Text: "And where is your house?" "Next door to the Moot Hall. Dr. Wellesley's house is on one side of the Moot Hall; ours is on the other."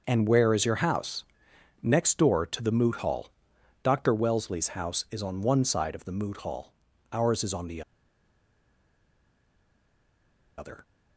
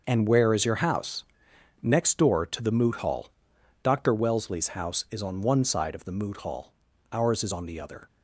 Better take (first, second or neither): second